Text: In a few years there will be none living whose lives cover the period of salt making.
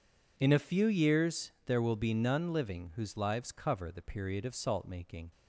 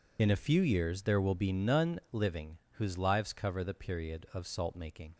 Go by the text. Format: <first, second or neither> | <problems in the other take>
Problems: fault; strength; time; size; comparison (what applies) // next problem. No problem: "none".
first | loses the start of "In"; at 0.1 s; 55 ms // pauses between "living" and "whose"; slight; at 2.5 s; 0.20 s long